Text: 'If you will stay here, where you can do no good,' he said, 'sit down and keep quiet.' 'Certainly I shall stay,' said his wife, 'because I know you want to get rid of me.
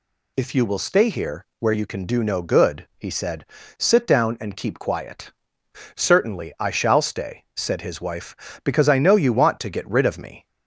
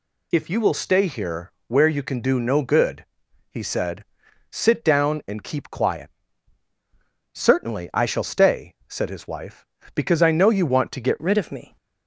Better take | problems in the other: first | changes voice at "rid"; from 11.2 s on; 0.5 s long

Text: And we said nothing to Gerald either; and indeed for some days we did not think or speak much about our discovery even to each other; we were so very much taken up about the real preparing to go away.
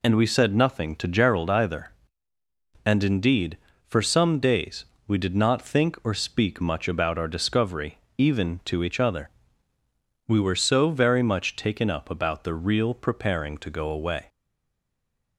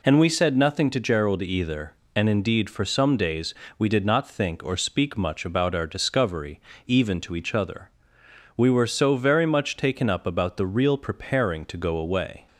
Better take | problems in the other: second | pauses between "days" and "we"; slight; at 4.8 s; 0.22 s long; slight in the second // pauses between "discovery" and "even"; slight; at 7.9 s; 0.20 s long; slight in the second // stays silent after the last word; from 14.2 s on; 1.1 s long

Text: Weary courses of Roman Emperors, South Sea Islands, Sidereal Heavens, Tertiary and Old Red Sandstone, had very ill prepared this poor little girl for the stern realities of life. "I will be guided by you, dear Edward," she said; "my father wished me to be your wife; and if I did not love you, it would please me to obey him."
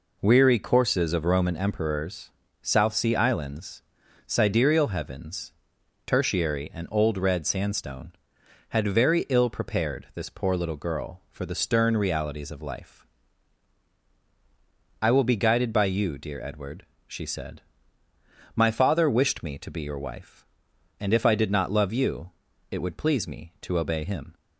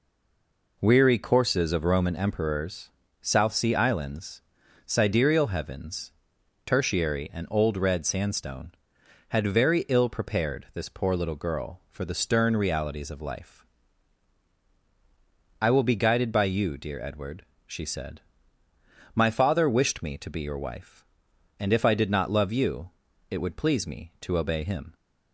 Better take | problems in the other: first | stays silent before the first word; slight; until 0.7 s; 0.7 s long

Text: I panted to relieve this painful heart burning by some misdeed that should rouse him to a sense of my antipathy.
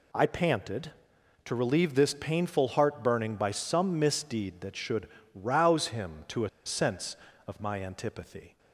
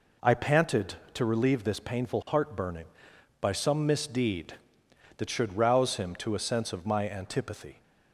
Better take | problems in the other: second | pauses between "should" and "rouse"; slight; at 5.0 s; 0.26 s long // pauses between "a" and "sense"; slight; at 6.4 s; 0.16 s long

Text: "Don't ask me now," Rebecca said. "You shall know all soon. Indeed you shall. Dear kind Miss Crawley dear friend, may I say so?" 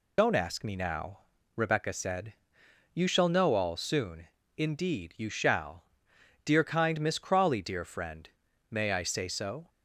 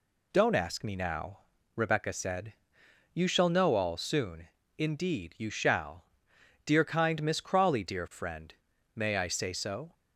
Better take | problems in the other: second | loses the start of "Don't"; at 0.1 s; 55 ms

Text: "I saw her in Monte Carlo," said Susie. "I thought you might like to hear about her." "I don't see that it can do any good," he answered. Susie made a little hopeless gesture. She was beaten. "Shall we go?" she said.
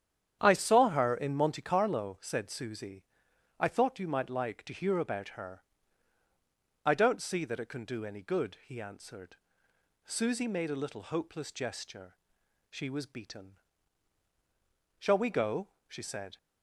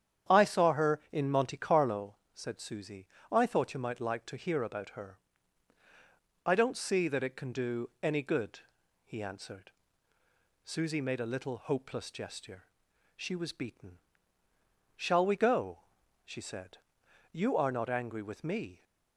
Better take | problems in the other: first | starts louder than the rest; strong; until 1.4 s; 9 dB; strong in the first // goes on to say "You are not angry with me"; from 17.3 s on; 1.5 s long

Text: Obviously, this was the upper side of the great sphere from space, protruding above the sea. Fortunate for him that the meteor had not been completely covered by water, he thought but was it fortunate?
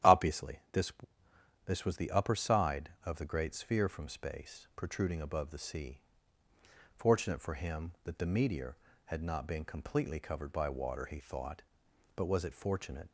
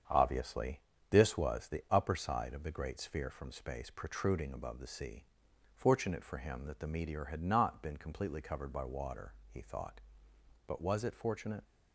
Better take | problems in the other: second | starts louder than the rest; strong; until 1.9 s; 11 dB; strong in the second // says "this" twice; at 1.6 s

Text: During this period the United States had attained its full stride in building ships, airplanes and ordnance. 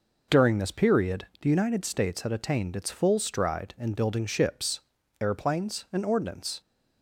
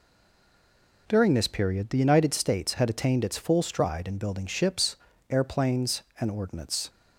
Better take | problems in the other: first | stays silent before the first word; until 1.0 s; 1.0 s long

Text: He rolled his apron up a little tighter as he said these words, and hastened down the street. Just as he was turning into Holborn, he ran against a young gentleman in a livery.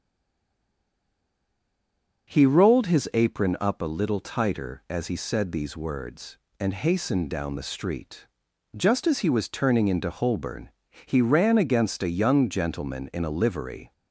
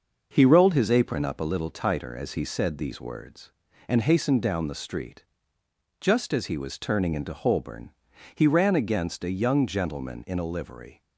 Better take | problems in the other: second | stays silent before the first word; until 2.2 s; 2.2 s long // starts louder than the rest; until 3.3 s; 6.5 dB

